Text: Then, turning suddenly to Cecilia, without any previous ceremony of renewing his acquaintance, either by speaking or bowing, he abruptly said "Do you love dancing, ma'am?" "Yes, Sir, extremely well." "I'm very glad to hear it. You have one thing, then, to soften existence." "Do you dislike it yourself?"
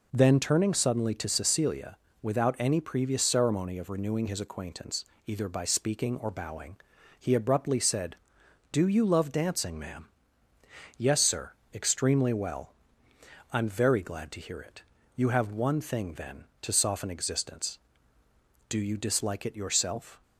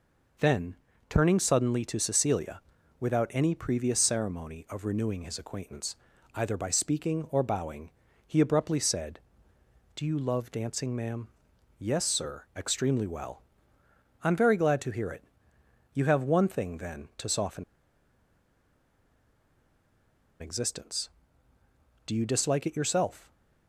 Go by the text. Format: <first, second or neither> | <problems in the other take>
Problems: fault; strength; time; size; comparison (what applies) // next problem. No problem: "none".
first | pauses between "soften" and "existence"; strong; at 17.6 s; 2.7 s long